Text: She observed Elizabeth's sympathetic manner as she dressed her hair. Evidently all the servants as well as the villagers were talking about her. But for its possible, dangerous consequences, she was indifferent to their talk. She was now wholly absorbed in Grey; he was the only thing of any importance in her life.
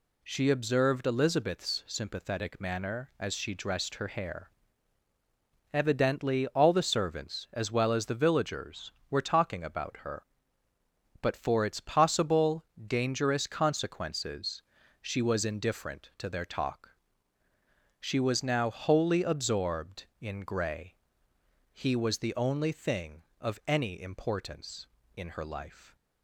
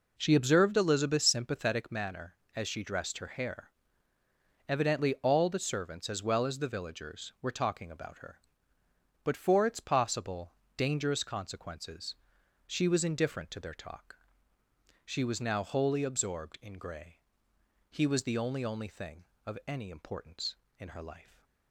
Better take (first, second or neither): first